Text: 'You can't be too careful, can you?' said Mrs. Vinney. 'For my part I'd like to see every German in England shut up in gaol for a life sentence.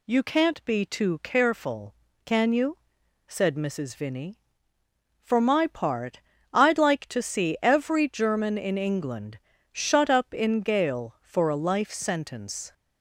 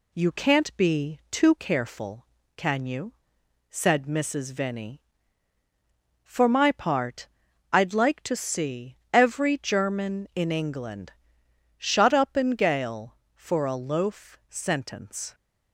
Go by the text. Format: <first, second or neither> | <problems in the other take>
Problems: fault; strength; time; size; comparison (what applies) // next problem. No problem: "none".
first | pauses between "part" and "I'd"; at 7.2 s; 0.44 s long; slight in the first // pauses between "England" and "shut"; noticeable; at 11.1 s; 0.66 s long; slight in the first // says "loaf" for "life"; at 13.7 s